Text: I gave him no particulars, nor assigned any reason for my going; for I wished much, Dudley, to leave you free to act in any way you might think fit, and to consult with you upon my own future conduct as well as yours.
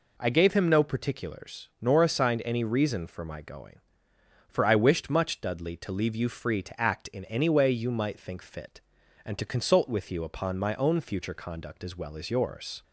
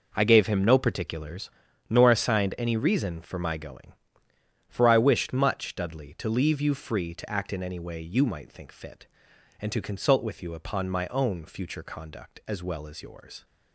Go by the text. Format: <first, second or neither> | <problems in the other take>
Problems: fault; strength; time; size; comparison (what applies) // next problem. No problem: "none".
neither | none